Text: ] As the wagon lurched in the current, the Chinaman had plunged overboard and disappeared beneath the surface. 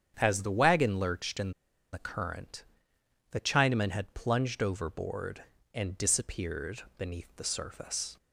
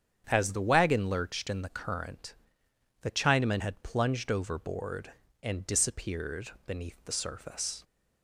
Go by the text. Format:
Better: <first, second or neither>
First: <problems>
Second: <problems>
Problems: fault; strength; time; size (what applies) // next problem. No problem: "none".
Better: second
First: starts louder than the rest; strong; until 1.1 s; 8 dB // pauses between "in" and "the"; at 1.5 s; 0.41 s long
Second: starts louder than the rest; strong; until 1.2 s; 8 dB